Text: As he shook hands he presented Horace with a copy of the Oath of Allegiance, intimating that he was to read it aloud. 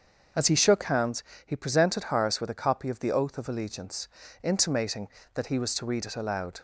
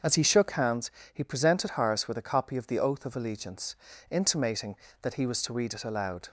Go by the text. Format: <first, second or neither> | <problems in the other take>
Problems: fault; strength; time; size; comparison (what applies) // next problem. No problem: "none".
neither | starts louder than the rest; the same in both // pauses between "hands" and "he"; slight; the same in both